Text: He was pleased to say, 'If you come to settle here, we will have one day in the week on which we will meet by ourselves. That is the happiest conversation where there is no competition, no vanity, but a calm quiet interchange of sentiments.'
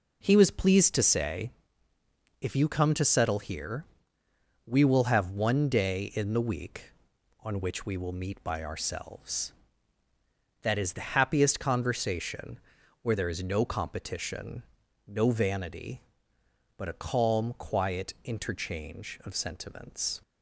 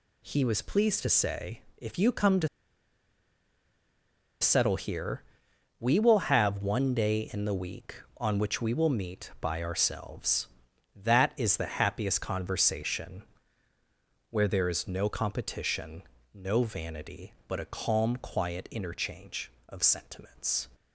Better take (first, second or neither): first